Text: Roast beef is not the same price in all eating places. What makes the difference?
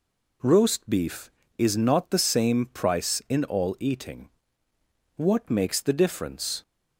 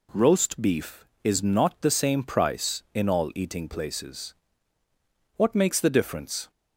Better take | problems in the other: second | skips "places"; at 4.7 s

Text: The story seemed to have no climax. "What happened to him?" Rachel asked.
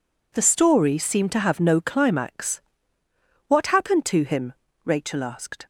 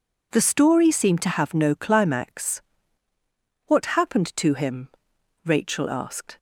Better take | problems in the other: neither | none

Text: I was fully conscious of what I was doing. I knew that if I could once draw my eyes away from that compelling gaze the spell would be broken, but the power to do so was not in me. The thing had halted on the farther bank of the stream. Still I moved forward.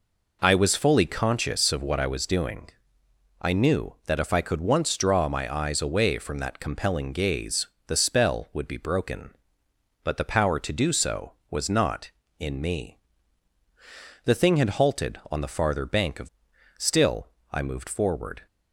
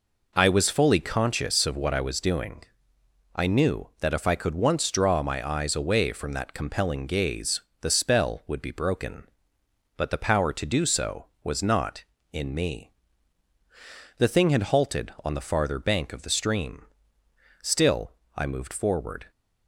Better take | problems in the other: second | pauses between "gaze" and "the"; slight; at 7.6 s; 0.20 s long; slight in the second // skips "the stream"; at 16.5 s // pauses between "Still" and "I"; slight; at 17.2 s; 0.24 s long; slight in the second

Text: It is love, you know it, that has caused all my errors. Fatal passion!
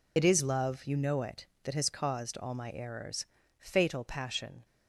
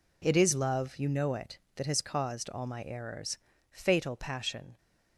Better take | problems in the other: second | loses the start of "It"; at 0.1 s; 60 ms

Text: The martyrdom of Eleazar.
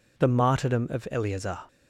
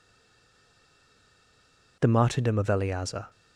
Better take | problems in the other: first | stays silent before the first word; noticeable; until 1.9 s; 1.9 s long

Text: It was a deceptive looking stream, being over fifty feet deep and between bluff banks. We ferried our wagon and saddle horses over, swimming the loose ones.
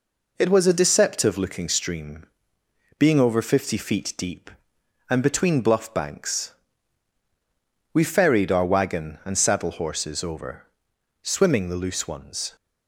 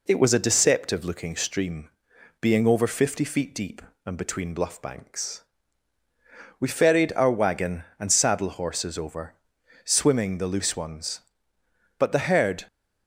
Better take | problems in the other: first | goes on to say "But the herd"; noticeable; from 11.9 s on; 0.68 s long

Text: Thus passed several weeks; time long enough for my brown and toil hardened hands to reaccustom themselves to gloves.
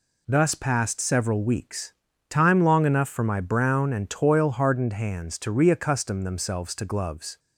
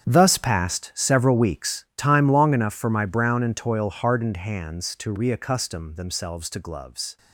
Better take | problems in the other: first | gets quieter; strong; throughout; 14 dB

